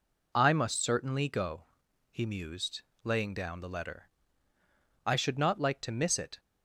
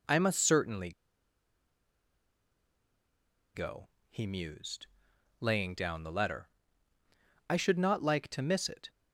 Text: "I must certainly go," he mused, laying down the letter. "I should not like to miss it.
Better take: first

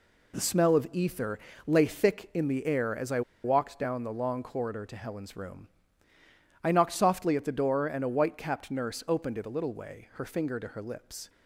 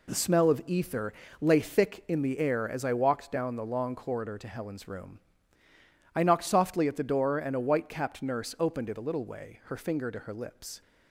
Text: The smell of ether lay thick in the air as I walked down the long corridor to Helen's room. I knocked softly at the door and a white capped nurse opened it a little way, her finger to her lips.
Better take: second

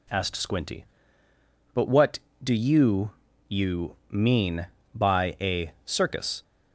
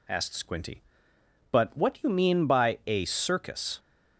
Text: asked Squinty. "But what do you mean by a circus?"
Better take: second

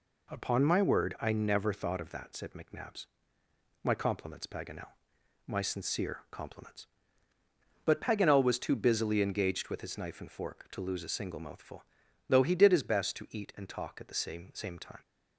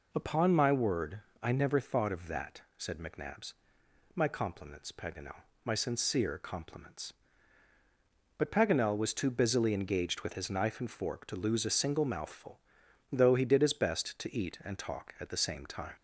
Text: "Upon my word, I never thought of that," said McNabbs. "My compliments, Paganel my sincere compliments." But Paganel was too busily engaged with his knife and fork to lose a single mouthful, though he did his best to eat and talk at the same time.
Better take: second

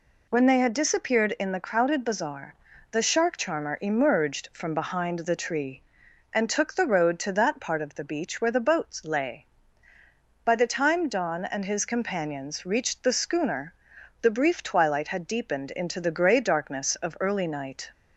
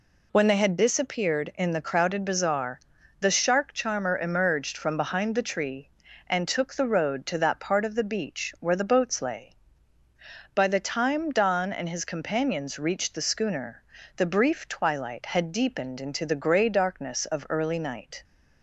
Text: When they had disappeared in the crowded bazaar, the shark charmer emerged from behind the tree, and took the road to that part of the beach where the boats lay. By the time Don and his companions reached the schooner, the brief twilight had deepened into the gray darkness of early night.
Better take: neither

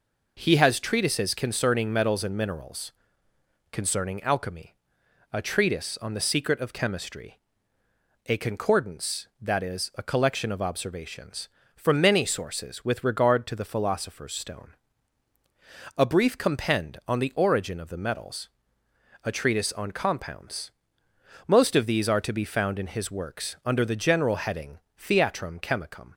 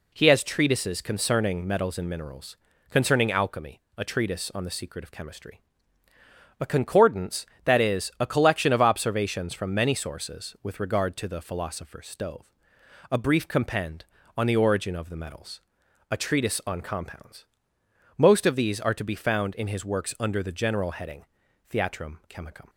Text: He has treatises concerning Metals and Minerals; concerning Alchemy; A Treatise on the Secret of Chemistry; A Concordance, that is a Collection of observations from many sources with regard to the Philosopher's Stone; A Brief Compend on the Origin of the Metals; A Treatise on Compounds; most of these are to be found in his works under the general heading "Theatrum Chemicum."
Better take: first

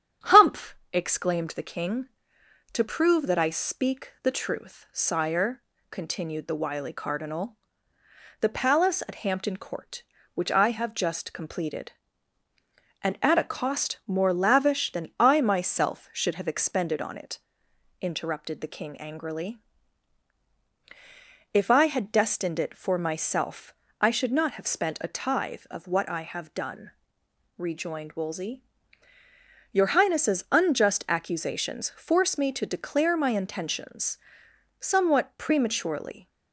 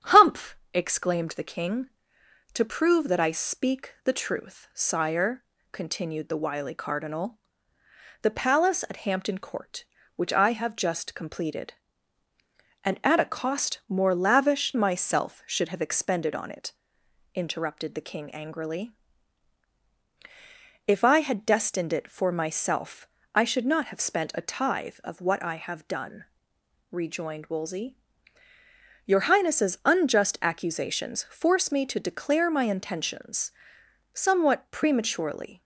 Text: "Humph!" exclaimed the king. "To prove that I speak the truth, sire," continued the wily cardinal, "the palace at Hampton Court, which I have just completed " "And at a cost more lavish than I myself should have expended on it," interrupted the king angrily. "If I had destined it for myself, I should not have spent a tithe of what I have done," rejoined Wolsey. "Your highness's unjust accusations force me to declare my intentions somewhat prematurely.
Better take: first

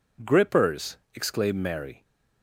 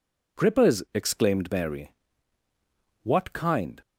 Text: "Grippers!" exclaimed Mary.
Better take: first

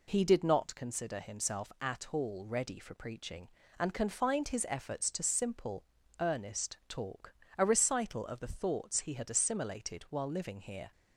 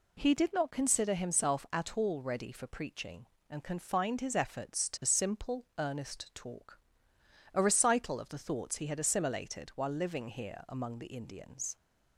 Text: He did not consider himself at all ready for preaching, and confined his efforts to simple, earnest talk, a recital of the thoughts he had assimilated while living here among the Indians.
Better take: second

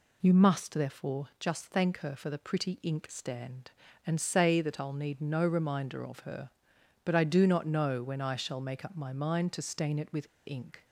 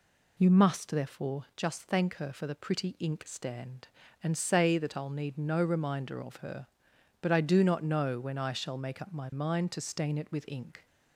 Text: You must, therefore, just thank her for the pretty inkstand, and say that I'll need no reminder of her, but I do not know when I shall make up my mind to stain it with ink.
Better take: second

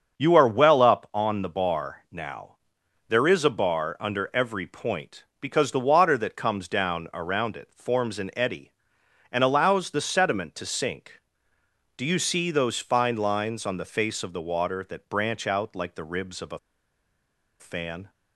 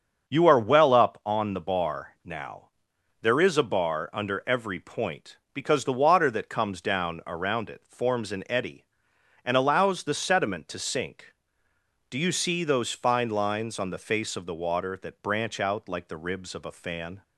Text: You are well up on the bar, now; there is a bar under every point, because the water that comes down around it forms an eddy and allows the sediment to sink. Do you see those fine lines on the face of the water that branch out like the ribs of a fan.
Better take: second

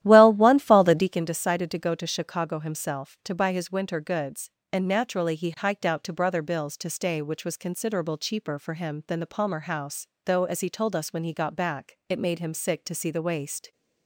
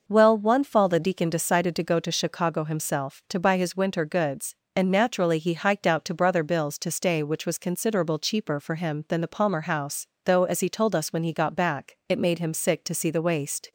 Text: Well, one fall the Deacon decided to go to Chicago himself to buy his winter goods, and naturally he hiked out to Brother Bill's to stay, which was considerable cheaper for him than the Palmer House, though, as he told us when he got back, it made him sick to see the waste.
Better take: second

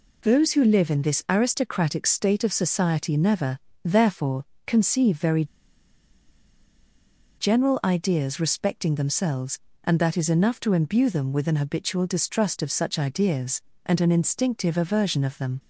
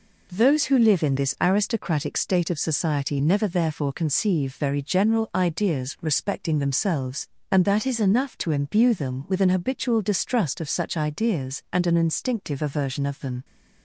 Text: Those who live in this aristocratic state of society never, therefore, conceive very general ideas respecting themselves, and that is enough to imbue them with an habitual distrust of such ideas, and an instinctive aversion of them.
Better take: second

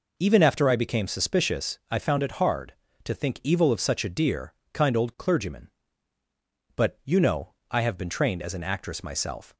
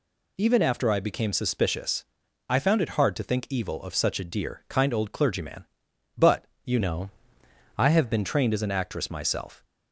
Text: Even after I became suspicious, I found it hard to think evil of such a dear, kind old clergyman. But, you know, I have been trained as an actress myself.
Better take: first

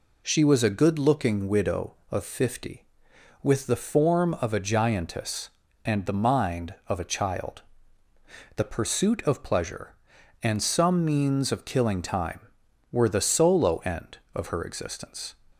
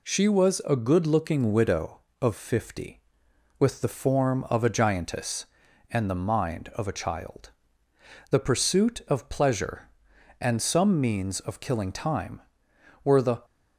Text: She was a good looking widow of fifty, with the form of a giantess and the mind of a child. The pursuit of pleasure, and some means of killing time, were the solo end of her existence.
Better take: first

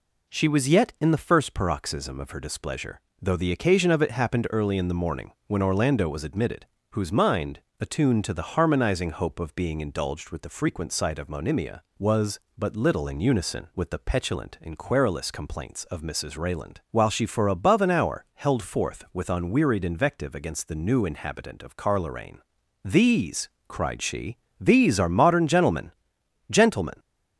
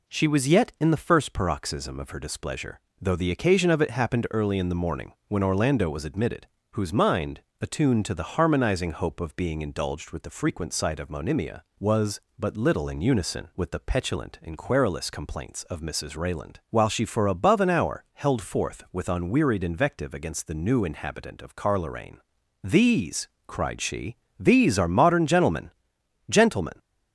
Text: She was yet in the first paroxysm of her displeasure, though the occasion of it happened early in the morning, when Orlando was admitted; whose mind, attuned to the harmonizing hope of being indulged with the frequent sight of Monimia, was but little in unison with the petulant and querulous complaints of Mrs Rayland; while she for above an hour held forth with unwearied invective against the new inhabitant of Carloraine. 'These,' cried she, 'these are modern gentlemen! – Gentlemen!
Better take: neither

